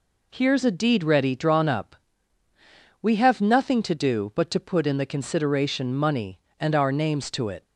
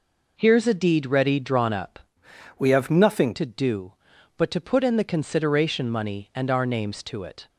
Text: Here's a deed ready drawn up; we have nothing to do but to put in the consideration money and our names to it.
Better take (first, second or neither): first